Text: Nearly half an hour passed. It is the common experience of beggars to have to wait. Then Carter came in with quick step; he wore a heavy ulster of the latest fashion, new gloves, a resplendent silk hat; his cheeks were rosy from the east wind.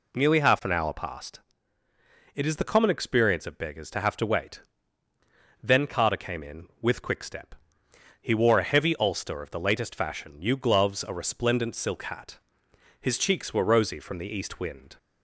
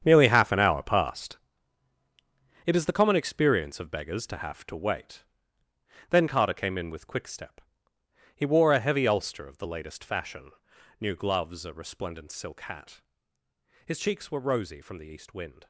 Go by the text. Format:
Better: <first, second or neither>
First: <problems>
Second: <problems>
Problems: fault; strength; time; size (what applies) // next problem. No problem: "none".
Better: first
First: none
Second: gets quieter; strong; throughout; 14 dB